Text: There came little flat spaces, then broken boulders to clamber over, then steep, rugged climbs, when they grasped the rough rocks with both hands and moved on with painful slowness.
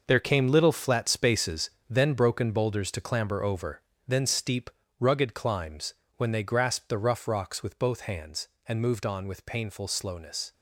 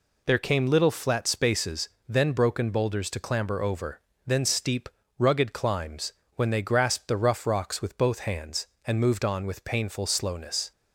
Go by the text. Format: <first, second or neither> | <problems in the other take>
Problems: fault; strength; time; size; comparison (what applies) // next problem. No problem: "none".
second | gets quieter; strong; throughout; 10.5 dB